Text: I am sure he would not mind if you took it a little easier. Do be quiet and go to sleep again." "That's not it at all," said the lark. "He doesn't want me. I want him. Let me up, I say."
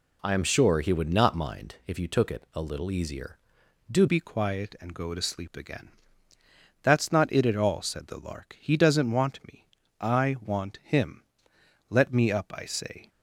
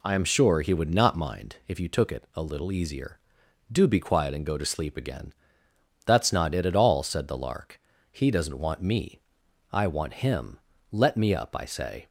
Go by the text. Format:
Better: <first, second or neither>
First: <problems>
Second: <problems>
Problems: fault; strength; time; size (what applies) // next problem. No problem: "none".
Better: second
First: changes voice at "be"; from 4.0 s on; 9.0 s long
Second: none